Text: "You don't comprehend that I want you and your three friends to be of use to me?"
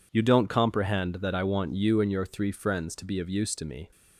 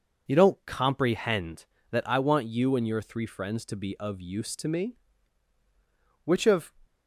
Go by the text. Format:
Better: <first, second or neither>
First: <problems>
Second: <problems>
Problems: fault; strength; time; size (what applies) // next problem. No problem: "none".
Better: first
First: none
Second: goes on to say "Which of"; slight; from 6.2 s on; 0.48 s long